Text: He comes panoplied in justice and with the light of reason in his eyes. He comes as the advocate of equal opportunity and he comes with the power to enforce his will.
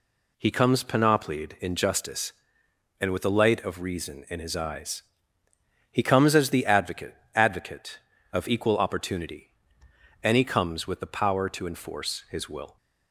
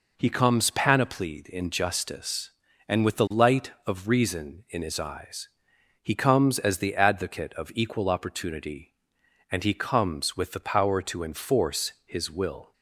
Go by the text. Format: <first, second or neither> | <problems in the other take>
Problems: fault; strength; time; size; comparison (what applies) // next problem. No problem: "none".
second | says "advocate" twice; at 7.3 s